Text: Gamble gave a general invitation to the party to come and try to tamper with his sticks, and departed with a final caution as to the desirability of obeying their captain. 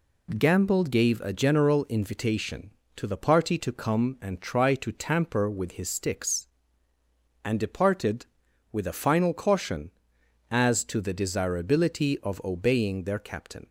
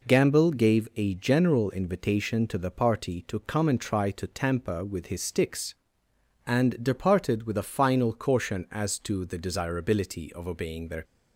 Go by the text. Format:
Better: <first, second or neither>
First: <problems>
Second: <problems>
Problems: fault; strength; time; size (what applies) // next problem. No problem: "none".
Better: first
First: none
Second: stops before "captain"; at 11.0 s